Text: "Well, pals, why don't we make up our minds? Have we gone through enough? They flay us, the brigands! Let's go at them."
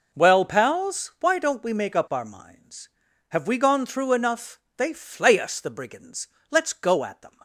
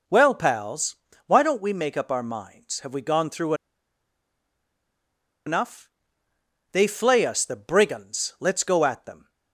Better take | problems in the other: first | pauses between "through" and "enough"; strong; at 3.5 s; 1.9 s long

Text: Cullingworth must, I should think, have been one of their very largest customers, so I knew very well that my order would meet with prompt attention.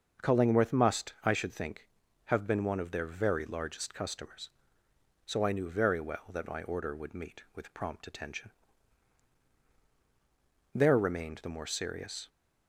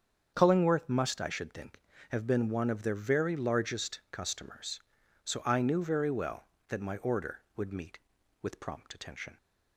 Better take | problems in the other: second | starts louder than the rest; until 1.3 s; 6.5 dB; strong in the second // goes on to say "There remained the more serious"; from 10.7 s on; 1.5 s long

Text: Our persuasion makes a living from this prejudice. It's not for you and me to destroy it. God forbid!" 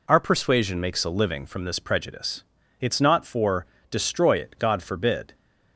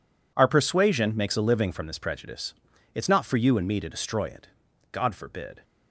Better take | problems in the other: second | skips "you and me to"; at 3.7 s

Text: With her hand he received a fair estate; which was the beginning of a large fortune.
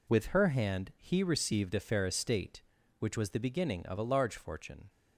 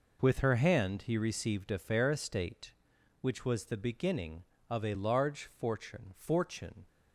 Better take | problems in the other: first | says "fortune" twice; at 6.1 s

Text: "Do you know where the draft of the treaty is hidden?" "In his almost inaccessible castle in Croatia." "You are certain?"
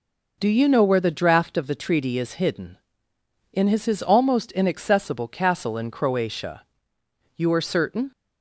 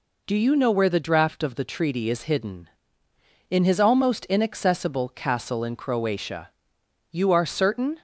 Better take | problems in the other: second | says "his" twice; at 3.8 s

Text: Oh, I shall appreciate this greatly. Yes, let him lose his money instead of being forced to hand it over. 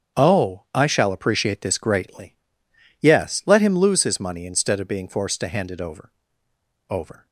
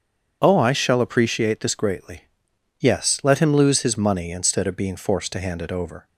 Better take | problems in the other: second | starts louder than the rest; strong; until 1.2 s; 7.5 dB; strong in the second // says "over" twice; at 6.8 s

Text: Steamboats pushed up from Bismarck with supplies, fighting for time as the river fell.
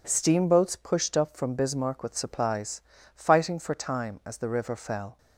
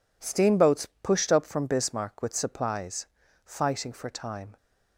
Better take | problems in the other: first | pauses between "Steamboats" and "pushed"; slight; at 0.8 s; 0.16 s long // stops before "as the river fell"; at 4.5 s

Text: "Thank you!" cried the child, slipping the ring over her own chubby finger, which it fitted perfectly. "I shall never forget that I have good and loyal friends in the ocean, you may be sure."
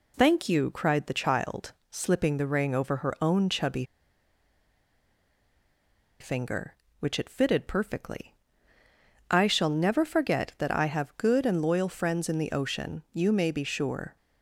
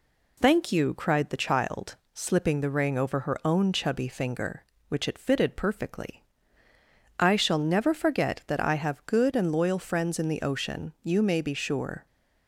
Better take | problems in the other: second | pauses between "chubby" and "finger"; strong; at 3.8 s; 2.3 s long

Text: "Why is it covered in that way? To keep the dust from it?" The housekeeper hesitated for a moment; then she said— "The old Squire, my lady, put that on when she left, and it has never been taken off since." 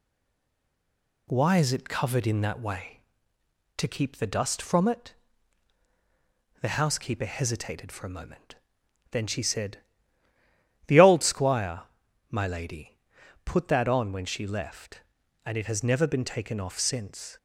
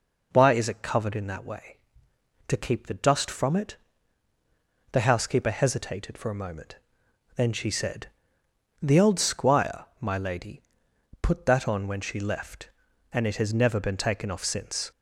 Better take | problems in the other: second | stays silent before the first word; noticeable; until 1.2 s; 1.2 s long

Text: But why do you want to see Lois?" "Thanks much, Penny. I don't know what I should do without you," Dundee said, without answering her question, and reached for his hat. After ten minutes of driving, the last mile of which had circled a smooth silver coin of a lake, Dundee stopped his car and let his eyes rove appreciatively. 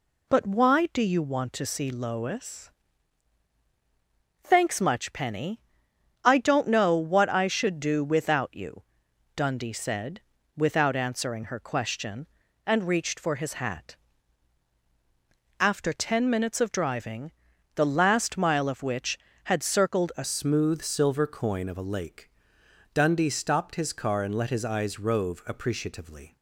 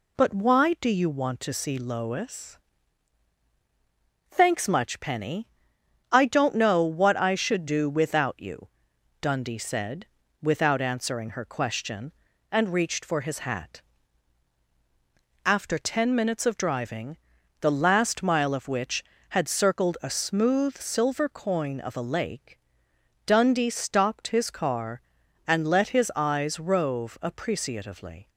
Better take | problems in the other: second | changes voice at "smooth"; from 20.2 s on; 6.1 s long

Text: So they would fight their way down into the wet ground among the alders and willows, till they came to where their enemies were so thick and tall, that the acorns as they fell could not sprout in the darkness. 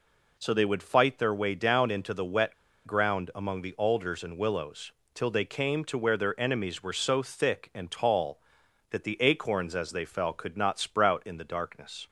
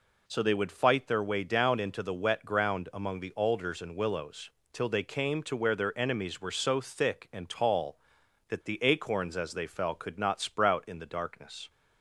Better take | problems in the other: second | pauses between "wet" and "ground"; slight; at 2.5 s; 0.31 s long

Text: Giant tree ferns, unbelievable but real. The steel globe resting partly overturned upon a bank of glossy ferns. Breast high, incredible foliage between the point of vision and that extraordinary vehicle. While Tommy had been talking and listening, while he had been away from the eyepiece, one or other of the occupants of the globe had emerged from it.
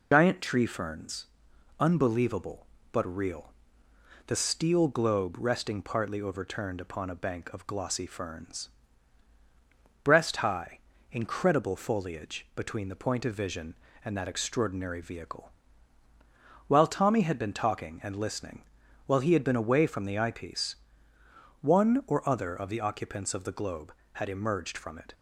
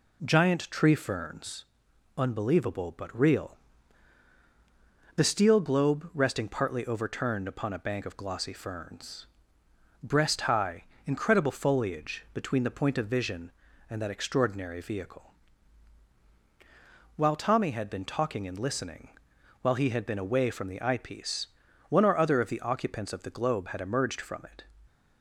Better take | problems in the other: second | loses the start of "Giant"; at 0.1 s; 85 ms

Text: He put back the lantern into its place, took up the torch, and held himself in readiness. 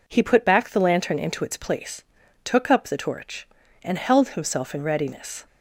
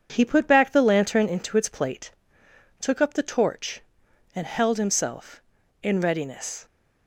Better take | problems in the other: first | says "plate" for "place"; at 1.6 s

